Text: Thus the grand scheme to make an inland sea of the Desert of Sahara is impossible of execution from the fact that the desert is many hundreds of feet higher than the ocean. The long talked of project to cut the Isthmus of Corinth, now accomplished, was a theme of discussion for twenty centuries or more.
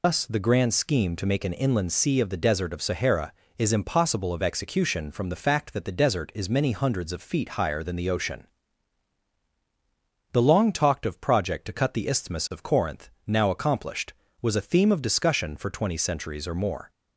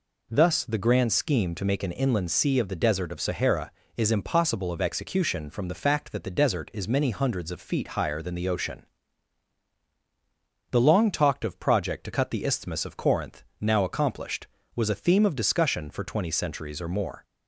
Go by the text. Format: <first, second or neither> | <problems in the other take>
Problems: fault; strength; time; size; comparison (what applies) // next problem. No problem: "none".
second | loses the start of "Thus"; at 0.0 s; 135 ms